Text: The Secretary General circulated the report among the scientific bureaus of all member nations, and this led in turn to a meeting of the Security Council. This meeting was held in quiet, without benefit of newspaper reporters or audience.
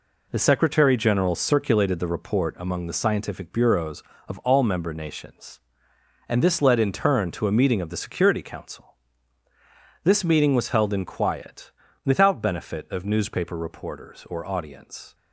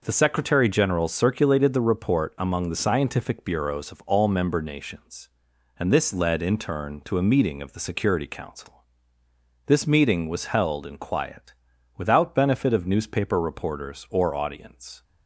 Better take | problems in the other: neither | none

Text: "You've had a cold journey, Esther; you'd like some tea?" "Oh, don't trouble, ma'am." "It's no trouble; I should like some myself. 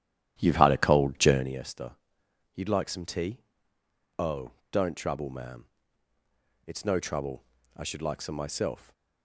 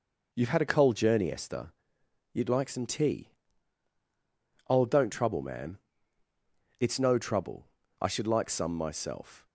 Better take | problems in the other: second | starts louder than the rest; strong; until 1.6 s; 11.5 dB

